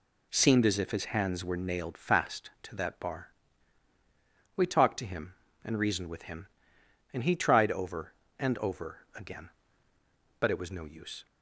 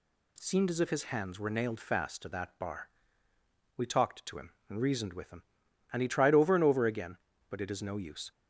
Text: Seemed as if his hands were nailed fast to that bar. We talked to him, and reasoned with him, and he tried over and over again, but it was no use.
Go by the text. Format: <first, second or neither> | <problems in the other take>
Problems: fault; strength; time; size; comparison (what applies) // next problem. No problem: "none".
first | says "is" for "was"; at 7.7 s